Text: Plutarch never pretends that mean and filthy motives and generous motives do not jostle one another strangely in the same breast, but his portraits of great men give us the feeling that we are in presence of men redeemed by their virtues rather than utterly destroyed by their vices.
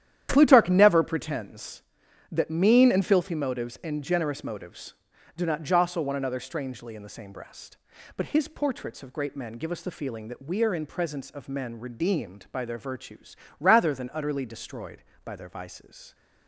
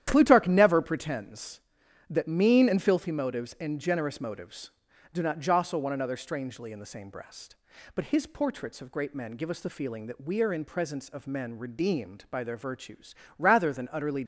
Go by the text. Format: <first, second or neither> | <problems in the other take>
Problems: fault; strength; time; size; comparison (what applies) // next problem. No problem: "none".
first | starts louder than the rest; strong; until 1.0 s; 11 dB; strong in the first // pauses between "virtues" and "rather"; slight; at 13.1 s; 0.22 s long; slight in the first // stops before "destroyed by their vices"; at 14.2 s